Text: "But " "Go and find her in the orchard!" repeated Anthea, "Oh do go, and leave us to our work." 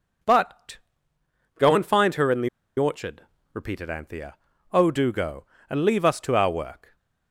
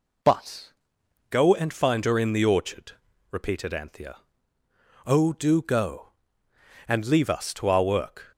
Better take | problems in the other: second | pauses between "the" and "orchard"; slight; at 2.4 s; 0.30 s long

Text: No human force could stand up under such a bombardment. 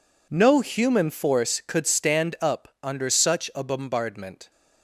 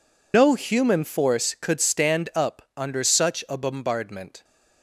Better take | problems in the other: first | loses the start of "No"; at 0.3 s; 105 ms

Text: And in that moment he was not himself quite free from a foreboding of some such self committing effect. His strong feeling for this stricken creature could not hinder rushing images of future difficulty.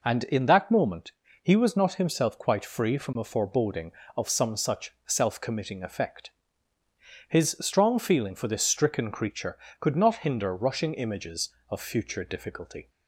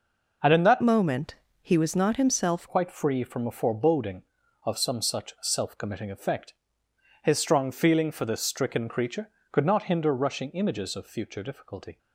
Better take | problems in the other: first | changes voice from "moment" to "himself"; from 0.8 to 2.6 s; 1.8 s long // pauses between "moment" and "he"; slight; at 1.3 s; 0.26 s long; slight in the first

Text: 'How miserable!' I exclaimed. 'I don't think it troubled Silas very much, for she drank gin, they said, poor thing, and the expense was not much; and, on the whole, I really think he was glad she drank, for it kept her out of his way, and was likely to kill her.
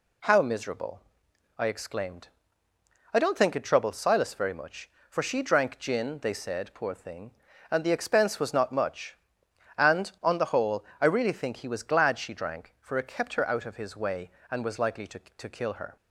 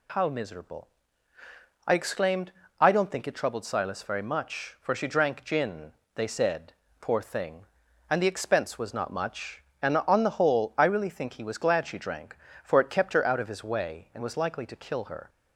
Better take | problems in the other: second | says "to" twice; at 15.1 s

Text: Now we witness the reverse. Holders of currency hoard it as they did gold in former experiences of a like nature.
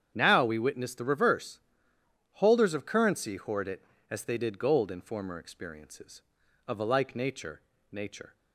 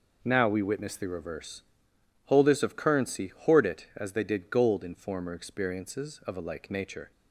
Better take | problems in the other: second | starts louder than the rest; strong; until 1.1 s; 8.5 dB // says "nature" twice; at 7.9 s

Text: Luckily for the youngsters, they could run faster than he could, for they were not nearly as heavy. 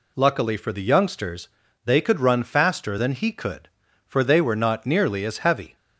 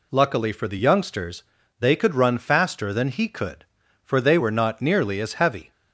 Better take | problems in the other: neither | none

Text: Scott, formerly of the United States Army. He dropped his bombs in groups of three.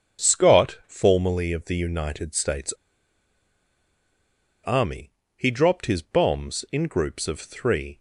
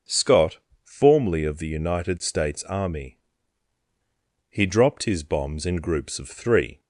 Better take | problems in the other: second | starts louder than the rest; until 1.3 s; 7 dB // pauses between "States" and "Army"; strong; at 2.7 s; 1.9 s long

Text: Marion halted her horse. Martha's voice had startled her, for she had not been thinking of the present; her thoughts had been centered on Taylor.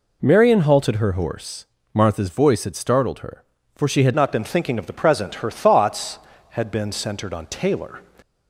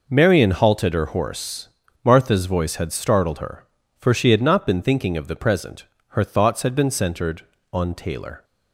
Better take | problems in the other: second | changes voice at "not"; from 4.1 s on; 3.9 s long

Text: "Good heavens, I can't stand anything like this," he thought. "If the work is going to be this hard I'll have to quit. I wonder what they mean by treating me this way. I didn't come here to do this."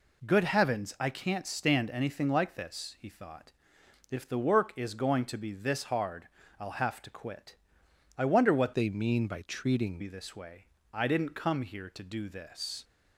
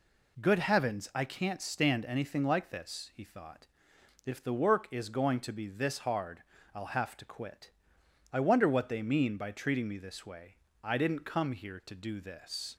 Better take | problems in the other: second | pauses between "hard" and "I'll"; slight; at 6.2 s; 0.32 s long; slight in the second // changes voice from "they" to "treating"; from 8.7 to 9.9 s; 1.2 s long

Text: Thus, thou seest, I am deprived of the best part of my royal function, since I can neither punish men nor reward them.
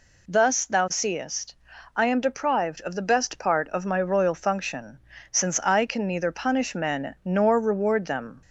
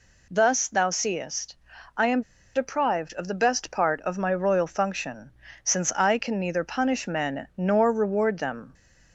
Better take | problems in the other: first | pauses between "am" and "deprived"; slight; at 2.2 s; 0.33 s long

